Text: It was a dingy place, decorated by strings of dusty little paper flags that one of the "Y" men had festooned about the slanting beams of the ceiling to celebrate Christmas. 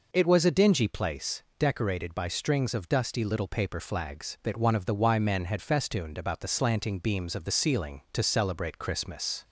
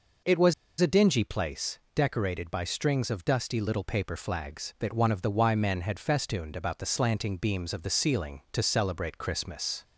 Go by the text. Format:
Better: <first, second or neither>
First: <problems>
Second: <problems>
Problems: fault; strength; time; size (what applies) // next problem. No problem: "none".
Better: first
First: none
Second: pauses between "was" and "a"; slight; at 0.5 s; 0.27 s long